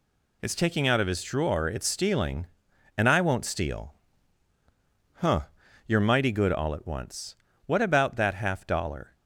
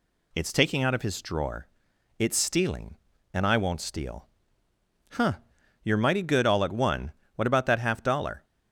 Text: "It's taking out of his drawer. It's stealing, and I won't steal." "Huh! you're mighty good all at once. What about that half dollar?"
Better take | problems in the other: first | says "one" for "once"; at 6.7 s

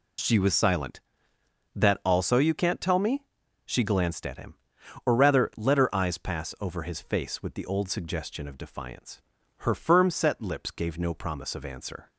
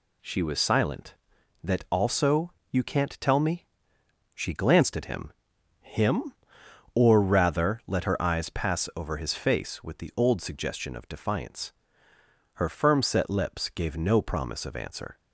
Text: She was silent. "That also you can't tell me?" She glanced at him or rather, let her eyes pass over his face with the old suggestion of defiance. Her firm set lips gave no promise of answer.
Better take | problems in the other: first | pauses between "also" and "you"; slight; at 2.5 s; 0.18 s long // says "him" twice; at 5.8 s

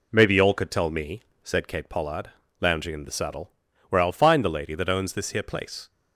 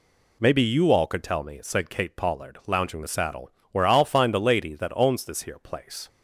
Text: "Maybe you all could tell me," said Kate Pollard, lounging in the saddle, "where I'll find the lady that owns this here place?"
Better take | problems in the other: first | skips "in"; at 3.0 s

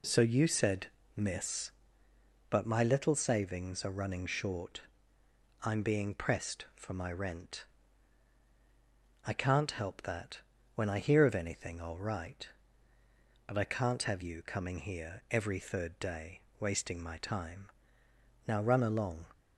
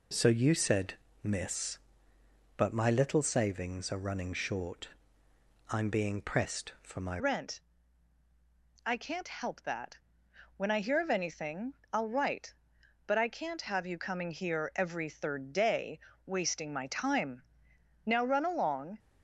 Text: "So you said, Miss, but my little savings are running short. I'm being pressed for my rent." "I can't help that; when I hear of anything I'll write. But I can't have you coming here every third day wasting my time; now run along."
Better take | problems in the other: first | changes voice at "rent"; from 7.1 s on; 11.8 s long // pauses between "anything" and "I'll"; slight; at 11.7 s; 0.20 s long // pauses between "day" and "wasting"; slight; at 16.0 s; 0.26 s long; slight in the first

